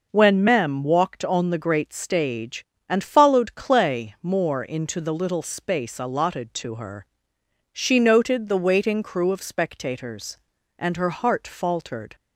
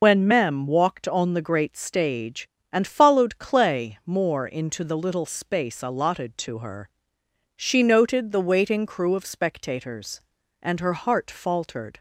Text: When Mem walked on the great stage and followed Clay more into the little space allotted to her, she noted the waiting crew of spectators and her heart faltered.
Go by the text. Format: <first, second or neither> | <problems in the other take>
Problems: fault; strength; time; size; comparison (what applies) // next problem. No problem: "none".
first | loses the start of "When"; at 0.0 s; 80 ms